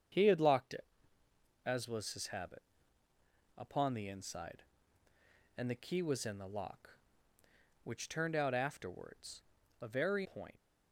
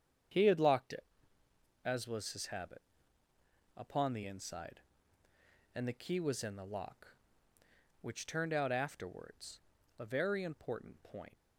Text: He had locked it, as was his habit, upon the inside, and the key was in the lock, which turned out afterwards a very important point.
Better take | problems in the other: second | starts louder than the rest; strong; until 1.9 s; 7.5 dB; strong in the second // pauses between "afterwards" and "a"; at 9.4 s; 0.40 s long; also in the second // skips "important"; at 10.2 s

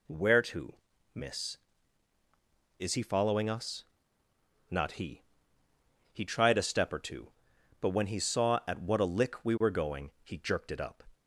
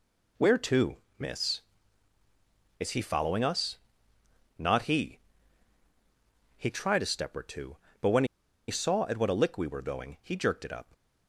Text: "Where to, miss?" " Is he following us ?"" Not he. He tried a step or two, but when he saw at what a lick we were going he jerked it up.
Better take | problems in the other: first | pauses between "when" and "he"; at 8.2 s; 0.42 s long

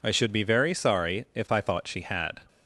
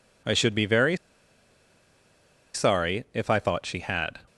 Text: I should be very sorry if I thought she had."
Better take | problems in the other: first | pauses between "very" and "sorry"; strong; at 0.9 s; 1.5 s long

